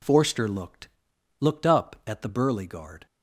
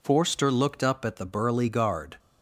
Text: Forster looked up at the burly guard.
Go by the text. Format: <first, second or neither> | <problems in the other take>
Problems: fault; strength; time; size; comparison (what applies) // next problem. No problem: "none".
second | says "looked" twice; at 1.4 s